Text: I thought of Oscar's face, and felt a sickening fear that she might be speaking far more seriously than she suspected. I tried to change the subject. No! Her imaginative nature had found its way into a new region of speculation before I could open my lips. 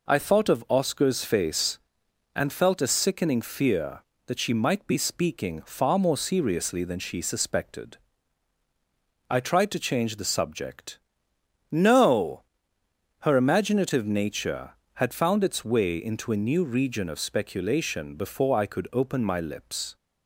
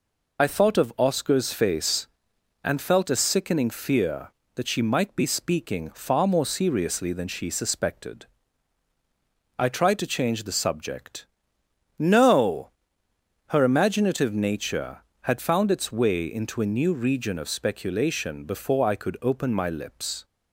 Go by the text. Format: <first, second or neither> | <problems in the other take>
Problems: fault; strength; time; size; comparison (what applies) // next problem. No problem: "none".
first | loses the start of "I"; at 0.3 s; 30 ms